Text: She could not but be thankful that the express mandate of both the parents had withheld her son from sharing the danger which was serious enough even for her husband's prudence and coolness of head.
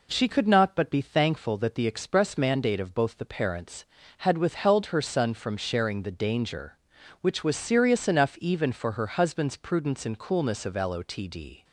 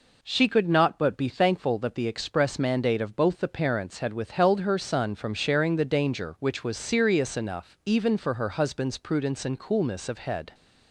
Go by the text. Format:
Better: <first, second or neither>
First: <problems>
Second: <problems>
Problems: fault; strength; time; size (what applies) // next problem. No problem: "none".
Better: second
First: says "lotd" for "head"; at 10.7 s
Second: none